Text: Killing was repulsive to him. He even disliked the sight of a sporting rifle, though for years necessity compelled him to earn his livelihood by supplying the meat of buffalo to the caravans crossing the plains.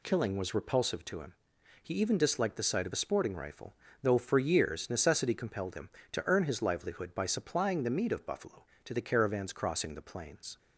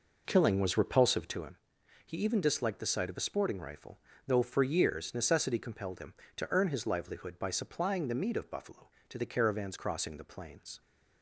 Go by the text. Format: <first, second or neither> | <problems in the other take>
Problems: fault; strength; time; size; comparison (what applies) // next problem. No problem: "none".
first | starts louder than the rest; noticeable; until 1.5 s; 5.5 dB